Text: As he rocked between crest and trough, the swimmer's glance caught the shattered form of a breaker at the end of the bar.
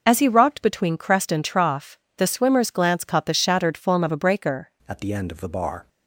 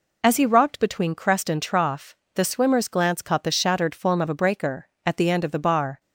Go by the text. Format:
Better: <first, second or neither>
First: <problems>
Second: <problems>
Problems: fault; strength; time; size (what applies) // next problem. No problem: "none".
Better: second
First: changes voice at "at"; from 4.8 s on; 1.0 s long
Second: none